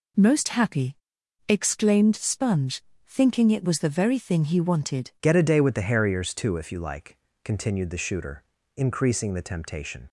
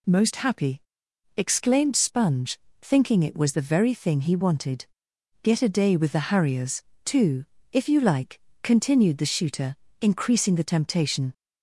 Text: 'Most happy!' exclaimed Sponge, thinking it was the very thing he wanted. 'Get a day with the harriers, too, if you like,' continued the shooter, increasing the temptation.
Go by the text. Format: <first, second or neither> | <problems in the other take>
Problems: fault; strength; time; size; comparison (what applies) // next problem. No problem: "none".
second | changes voice at "Get"; from 5.2 s on; 4.8 s long